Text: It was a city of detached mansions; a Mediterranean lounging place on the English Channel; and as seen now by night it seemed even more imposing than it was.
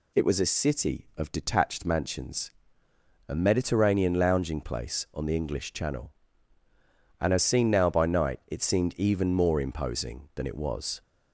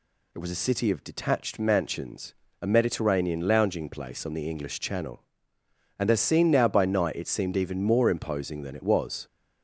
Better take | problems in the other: neither | none

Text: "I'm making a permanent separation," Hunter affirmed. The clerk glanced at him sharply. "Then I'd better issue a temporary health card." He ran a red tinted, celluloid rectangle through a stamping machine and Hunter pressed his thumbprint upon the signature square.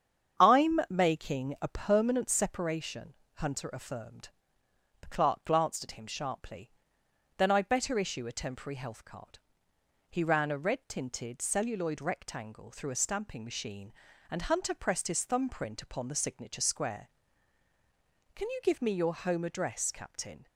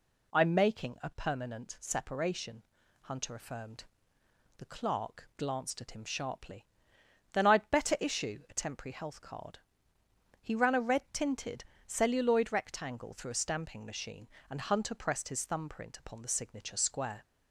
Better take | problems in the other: second | starts louder than the rest; strong; until 1.5 s; 8 dB // goes on to say "Can you give me your home address Captain"; strong; from 18.3 s on; 2.1 s long

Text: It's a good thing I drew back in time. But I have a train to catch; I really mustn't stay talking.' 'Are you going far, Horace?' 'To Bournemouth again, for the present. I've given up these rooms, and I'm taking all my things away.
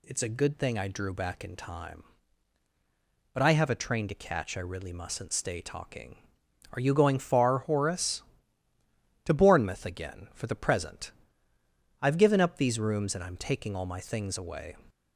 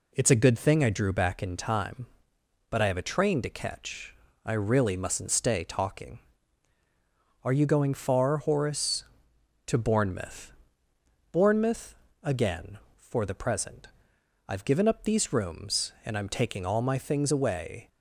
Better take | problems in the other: first | says "Bournemouth" twice; at 11.3 s

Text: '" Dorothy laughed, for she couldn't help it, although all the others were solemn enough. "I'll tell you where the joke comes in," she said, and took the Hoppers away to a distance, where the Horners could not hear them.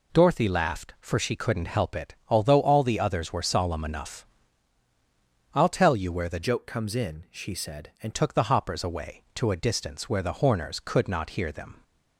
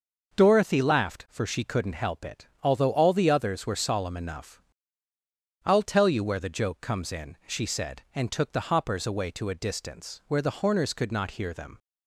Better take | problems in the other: second | changes voice from "joke" to "and"; from 6.4 to 8.1 s; 1.7 s long

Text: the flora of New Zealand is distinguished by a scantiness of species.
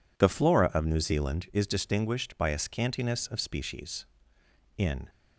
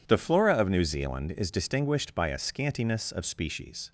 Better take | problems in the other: second | goes on to say "In"; slight; from 4.7 s on; 0.30 s long

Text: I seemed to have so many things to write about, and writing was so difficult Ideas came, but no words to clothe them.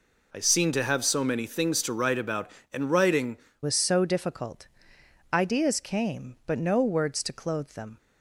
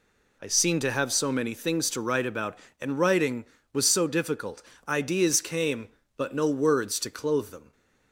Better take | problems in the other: second | changes voice at "was"; from 3.6 s on; 4.3 s long // pauses between "difficult" and "Ideas"; noticeable; at 4.6 s; 0.66 s long; slight in the second

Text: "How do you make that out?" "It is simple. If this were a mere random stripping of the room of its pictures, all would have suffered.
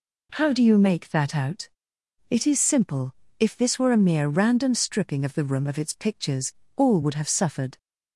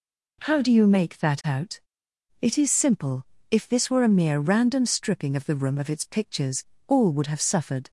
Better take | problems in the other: neither | none

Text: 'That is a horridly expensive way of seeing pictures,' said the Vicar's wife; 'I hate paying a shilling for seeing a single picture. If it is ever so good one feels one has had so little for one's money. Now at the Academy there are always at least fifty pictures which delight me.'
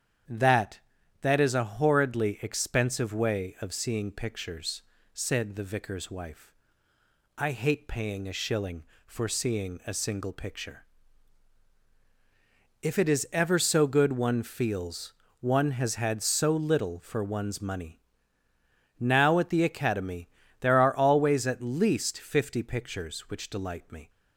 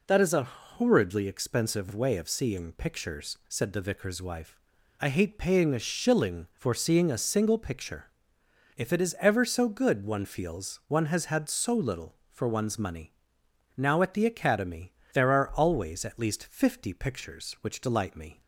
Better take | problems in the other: second | starts louder than the rest; strong; until 1.7 s; 9 dB // says "That" twice; at 1.2 s // pauses between "feels" and "one"; slight; at 15.1 s; 0.28 s long // pauses between "Academy" and "there"; slight; at 20.2 s; 0.34 s long; slight in the second

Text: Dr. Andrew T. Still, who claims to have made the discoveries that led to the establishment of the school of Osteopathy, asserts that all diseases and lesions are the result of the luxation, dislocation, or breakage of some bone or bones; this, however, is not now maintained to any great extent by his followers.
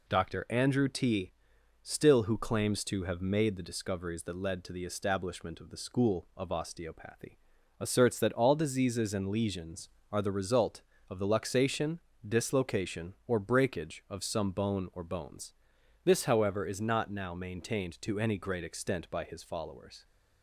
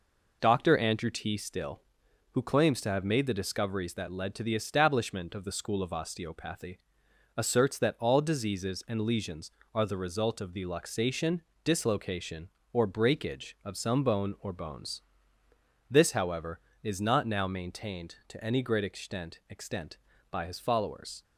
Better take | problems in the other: first | says "extent" twice; at 19.4 s

